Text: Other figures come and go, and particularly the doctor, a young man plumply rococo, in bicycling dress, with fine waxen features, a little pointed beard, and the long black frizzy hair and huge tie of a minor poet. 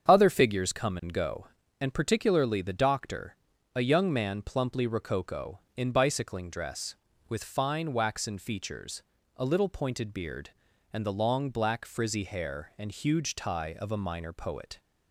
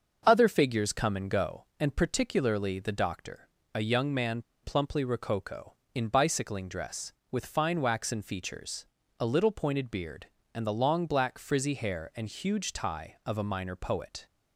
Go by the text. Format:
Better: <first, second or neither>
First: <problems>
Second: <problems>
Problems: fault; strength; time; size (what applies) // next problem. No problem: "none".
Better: first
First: starts louder than the rest; strong; until 1.1 s; 7.5 dB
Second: starts louder than the rest; until 1.2 s; 6.5 dB // pauses between "man" and "plumply"; slight; at 4.3 s; 0.22 s long